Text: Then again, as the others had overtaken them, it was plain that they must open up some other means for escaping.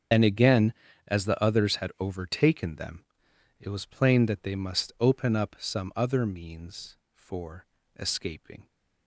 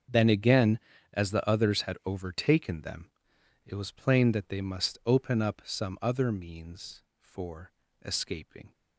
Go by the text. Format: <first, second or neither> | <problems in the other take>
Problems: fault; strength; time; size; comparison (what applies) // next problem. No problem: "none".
second | loses the start of "Then"; at 0.1 s; 85 ms // starts louder than the rest; strong; until 1.4 s; 7.5 dB; also in the second // pauses between "for" and "escaping"; slight; at 7.6 s; 0.32 s long; slight in the second